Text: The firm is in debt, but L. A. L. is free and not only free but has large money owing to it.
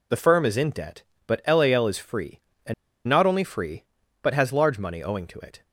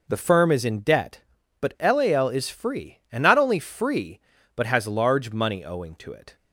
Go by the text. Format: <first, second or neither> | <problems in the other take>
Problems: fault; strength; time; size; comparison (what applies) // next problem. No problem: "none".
second | pauses between "and" and "not"; slight; at 2.7 s; 0.34 s long